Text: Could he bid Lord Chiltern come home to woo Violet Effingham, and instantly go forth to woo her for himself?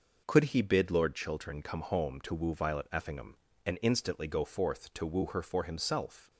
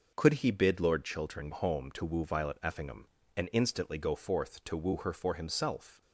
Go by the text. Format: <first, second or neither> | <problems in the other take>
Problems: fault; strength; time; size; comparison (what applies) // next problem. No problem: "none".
first | skips "come"; at 1.5 s